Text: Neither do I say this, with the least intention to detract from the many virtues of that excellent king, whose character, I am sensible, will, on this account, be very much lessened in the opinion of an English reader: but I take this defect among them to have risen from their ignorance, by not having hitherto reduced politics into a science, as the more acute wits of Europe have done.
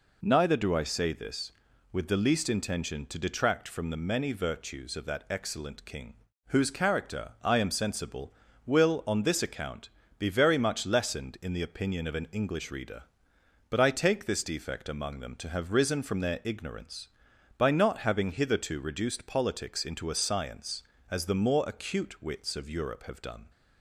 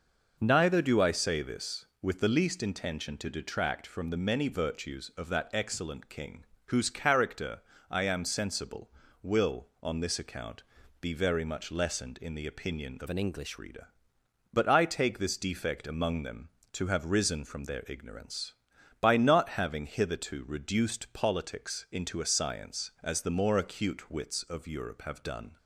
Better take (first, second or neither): first